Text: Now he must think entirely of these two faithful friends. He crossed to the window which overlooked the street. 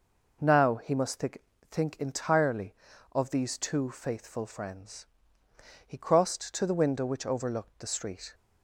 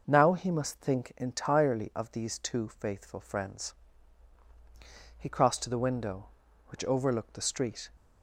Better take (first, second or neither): second